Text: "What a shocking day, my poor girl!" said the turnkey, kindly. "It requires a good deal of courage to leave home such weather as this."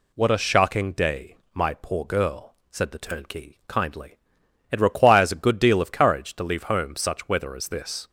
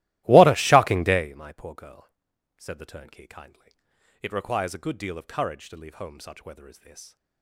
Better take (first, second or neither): first